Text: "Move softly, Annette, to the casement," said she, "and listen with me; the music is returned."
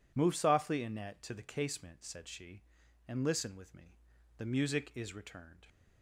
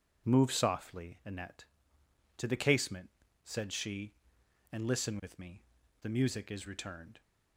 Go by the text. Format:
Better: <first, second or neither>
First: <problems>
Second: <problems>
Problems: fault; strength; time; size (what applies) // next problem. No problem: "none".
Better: neither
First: none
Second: none